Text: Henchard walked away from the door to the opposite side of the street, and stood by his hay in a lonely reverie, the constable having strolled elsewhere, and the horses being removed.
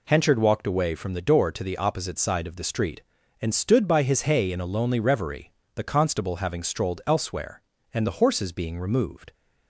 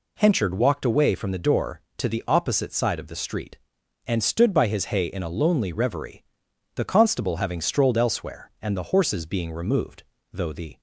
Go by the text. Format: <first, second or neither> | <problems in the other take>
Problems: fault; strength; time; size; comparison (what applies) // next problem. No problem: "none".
first | goes on to say "Though the"; slight; from 10.3 s on; 0.48 s long